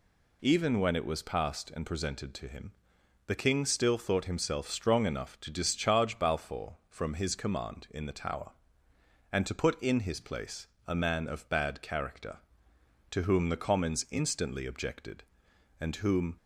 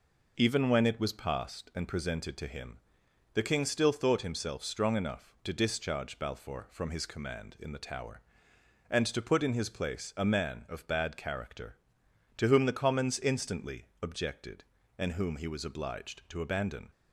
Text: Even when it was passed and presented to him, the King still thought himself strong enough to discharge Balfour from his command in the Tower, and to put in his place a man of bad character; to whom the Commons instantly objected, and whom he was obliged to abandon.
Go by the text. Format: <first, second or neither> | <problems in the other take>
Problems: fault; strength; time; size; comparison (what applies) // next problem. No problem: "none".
second | pauses between "place" and "a"; slight; at 10.6 s; 0.18 s long // stops before "he was obliged to abandon"; at 16.3 s